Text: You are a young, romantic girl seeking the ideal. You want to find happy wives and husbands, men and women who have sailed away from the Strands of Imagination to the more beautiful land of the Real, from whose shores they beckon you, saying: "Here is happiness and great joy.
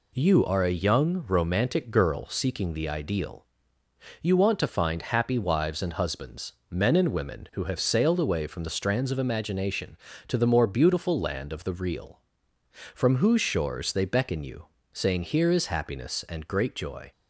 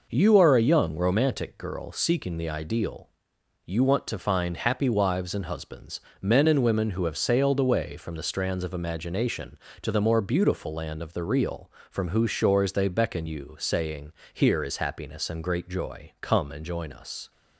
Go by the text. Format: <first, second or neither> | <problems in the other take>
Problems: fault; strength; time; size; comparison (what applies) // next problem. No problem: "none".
first | goes on to say "Come and join us"; noticeable; from 16.2 s on; 1.1 s long